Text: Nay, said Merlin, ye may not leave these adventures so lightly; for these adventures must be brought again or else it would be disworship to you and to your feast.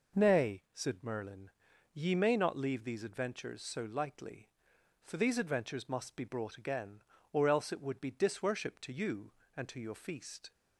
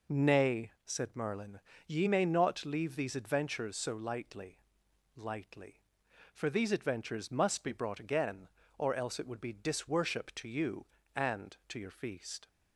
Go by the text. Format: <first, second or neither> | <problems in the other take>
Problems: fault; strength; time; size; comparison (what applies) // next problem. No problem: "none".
first | says "lightly" twice; at 5.1 s